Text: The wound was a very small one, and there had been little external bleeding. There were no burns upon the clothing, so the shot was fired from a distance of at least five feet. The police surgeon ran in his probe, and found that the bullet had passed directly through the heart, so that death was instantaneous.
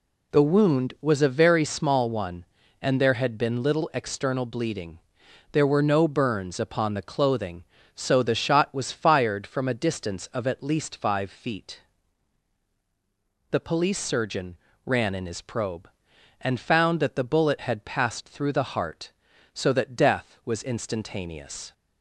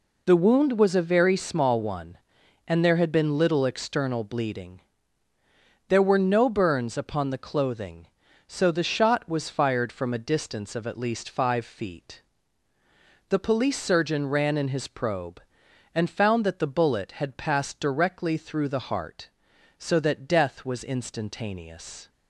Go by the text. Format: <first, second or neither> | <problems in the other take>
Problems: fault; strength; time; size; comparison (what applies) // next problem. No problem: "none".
second | pauses between "surgeon" and "ran"; slight; at 14.5 s; 0.28 s long // skips "directly"; at 18.2 s